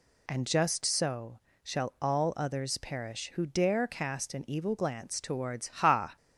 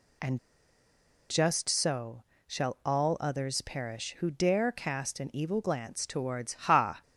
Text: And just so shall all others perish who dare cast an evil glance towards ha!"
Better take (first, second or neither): first